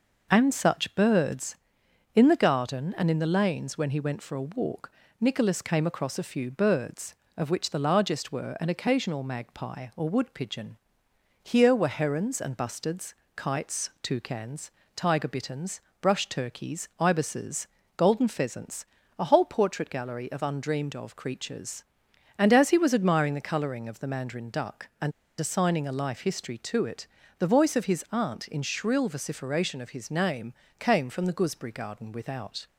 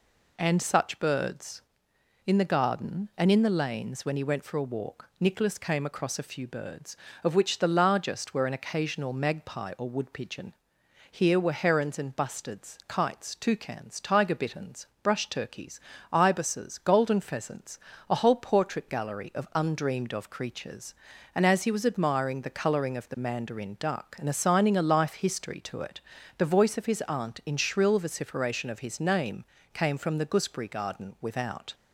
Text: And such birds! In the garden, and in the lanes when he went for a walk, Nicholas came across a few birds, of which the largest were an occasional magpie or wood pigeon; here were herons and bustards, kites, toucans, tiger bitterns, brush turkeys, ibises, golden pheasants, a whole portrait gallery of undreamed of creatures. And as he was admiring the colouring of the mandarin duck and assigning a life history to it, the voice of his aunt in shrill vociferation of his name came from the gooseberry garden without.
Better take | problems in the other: second | pauses between "and" and "assigning"; slight; at 25.1 s; 0.29 s long // pauses between "name" and "came"; slight; at 30.5 s; 0.26 s long; slight in the second

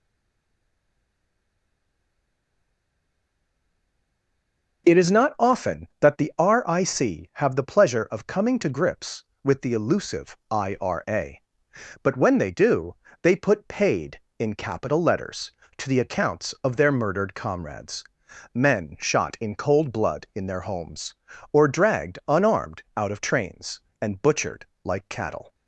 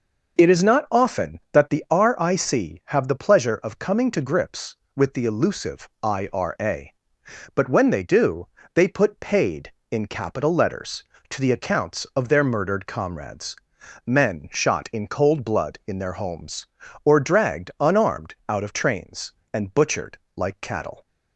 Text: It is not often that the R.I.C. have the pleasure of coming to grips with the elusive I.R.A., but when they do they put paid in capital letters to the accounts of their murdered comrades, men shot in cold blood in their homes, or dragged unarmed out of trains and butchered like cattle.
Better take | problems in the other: second | stays silent before the first word; strong; until 4.8 s; 4.8 s long // pauses between "do" and "they"; slight; at 12.9 s; 0.28 s long; slight in the second // pauses between "butchered" and "like"; slight; at 24.6 s; 0.18 s long; slight in the second

